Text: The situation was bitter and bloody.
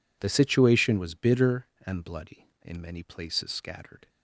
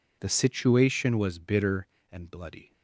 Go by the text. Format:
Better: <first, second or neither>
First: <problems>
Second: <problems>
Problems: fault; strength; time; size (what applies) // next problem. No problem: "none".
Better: second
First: goes on to say "In many places scattered"; from 2.6 s on; 1.4 s long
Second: none